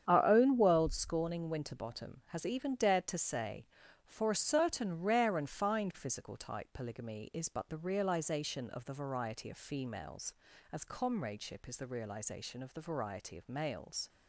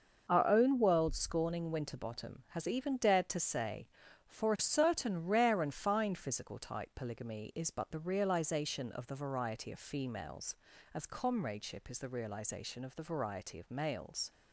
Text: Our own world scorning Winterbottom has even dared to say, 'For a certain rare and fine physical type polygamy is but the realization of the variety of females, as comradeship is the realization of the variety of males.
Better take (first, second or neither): second